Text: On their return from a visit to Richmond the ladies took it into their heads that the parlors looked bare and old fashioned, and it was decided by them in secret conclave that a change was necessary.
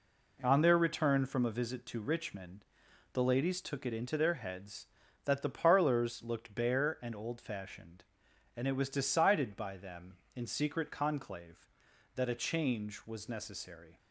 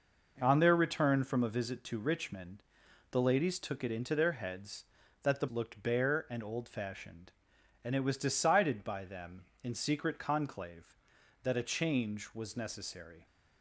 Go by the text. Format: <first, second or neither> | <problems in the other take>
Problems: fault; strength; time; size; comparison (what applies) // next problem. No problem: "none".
first | pauses between "Richmond" and "the"; noticeable; at 2.6 s; 0.50 s long; noticeable in the first // skips "parlors"; at 5.4 s